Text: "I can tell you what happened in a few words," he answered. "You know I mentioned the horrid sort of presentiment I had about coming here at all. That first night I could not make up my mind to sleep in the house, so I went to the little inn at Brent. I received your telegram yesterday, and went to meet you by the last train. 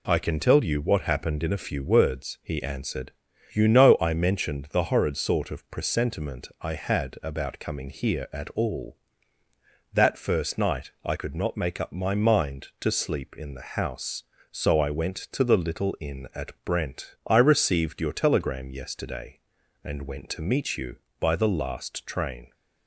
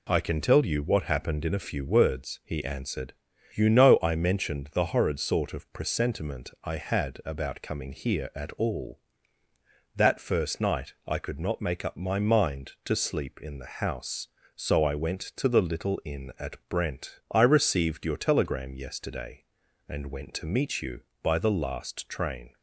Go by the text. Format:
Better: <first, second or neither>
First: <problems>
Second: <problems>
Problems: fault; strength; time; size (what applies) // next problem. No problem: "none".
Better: neither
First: none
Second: none